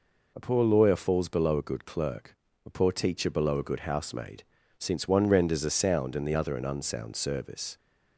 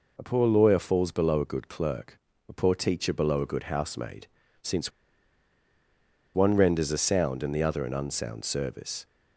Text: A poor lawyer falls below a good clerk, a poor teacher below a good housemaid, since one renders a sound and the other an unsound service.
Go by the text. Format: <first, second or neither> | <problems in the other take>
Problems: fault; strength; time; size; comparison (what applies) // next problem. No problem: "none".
first | pauses between "since" and "one"; strong; at 4.9 s; 1.4 s long